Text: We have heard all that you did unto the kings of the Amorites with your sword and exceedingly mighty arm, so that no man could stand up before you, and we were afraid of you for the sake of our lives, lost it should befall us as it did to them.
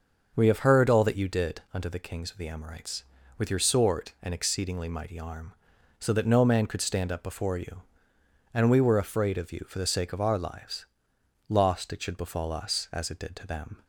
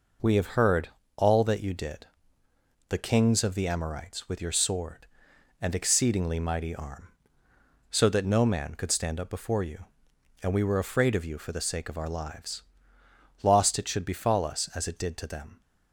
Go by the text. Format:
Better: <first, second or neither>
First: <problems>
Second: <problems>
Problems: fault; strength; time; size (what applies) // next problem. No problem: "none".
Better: first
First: none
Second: pauses between "heard" and "all"; slight; at 0.8 s; 0.28 s long // skips "unto"; at 2.4 s